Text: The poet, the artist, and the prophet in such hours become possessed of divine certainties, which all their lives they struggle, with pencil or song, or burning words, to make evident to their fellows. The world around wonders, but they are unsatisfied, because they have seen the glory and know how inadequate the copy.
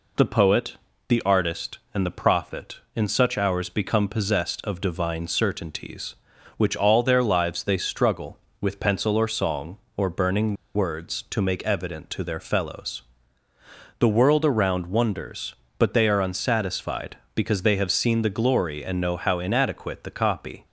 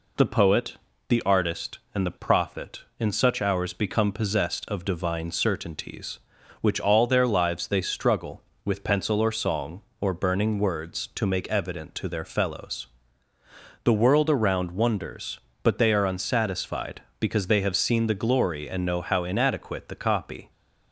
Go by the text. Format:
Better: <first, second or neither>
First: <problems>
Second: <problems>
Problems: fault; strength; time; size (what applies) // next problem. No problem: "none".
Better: second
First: pauses between "burning" and "words"; slight; at 10.5 s; 0.21 s long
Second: none